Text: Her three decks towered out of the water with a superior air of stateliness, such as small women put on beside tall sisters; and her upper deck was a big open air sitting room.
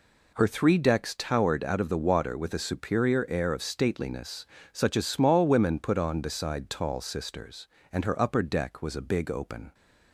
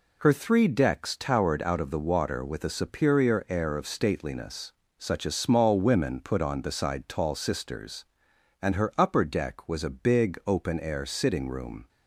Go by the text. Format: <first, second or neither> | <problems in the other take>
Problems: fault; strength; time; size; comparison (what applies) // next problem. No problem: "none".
second | stops before "air sitting room"; at 9.7 s